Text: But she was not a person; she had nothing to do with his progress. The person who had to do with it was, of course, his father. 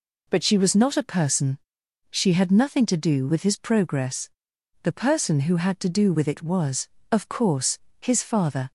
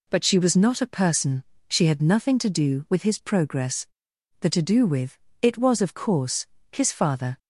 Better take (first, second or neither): first